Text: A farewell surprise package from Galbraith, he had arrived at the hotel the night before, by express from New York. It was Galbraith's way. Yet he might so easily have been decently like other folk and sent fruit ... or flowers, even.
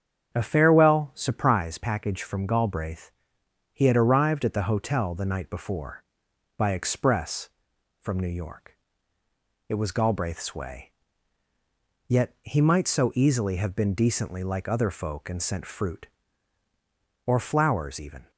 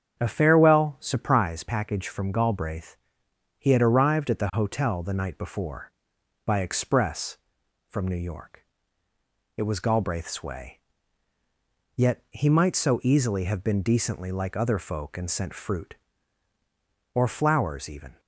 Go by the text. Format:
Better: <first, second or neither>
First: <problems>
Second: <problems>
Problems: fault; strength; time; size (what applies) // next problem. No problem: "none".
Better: neither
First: starts louder than the rest; strong; until 1.3 s; 8 dB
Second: starts louder than the rest; strong; until 1.2 s; 8 dB